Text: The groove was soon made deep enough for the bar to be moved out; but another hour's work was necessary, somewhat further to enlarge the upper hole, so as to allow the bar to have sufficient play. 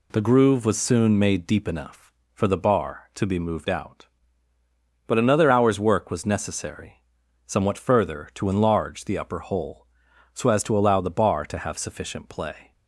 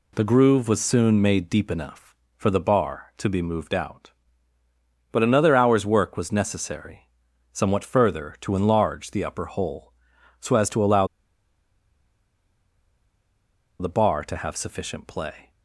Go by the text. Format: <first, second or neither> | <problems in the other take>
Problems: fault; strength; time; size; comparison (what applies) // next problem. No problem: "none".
first | pauses between "allow" and "the"; strong; at 11.0 s; 2.7 s long